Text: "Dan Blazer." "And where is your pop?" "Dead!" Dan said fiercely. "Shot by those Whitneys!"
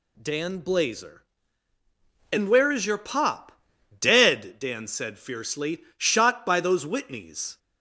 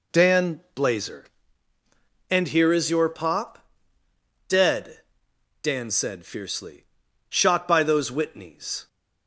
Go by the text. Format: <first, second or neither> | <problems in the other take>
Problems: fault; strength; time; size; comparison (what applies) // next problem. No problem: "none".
first | pauses between "Dan" and "Blazer"; slight; at 0.5 s; 0.16 s long // says "here" for "where"; at 2.4 s